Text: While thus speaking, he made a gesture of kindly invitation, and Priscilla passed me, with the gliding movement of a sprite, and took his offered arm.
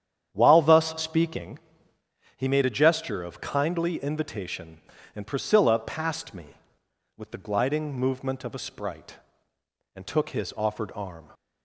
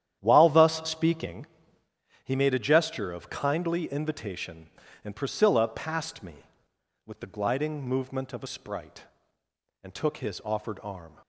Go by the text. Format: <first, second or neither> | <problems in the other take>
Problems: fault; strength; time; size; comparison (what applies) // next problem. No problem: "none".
first | gets quieter; strong; throughout; 12 dB // starts louder than the rest; strong; until 1.2 s; 10.5 dB; strong in the first